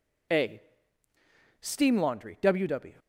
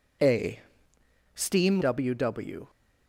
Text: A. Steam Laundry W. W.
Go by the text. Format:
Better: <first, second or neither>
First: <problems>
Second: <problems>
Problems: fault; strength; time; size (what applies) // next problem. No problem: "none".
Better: first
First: none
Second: skips "Laundry"; at 1.8 s